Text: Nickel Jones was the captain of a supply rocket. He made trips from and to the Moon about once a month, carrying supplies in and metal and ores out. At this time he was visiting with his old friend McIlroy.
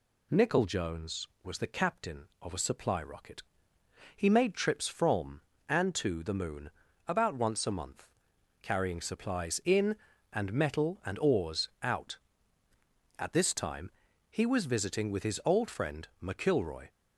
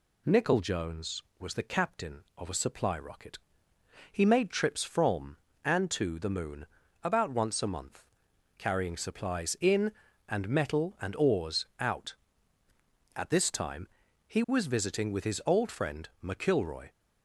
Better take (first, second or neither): neither